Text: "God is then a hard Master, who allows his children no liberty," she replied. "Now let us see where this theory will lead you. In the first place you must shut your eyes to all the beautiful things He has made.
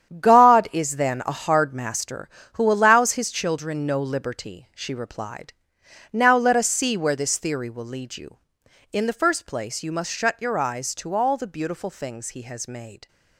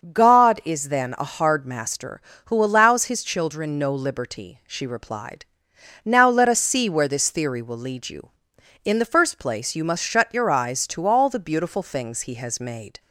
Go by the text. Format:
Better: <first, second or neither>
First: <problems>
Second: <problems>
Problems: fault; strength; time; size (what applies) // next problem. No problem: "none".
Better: second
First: gets quieter; strong; throughout; 10.5 dB // starts louder than the rest; strong; until 1.2 s; 9.5 dB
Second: starts louder than the rest; until 1.1 s; 6.5 dB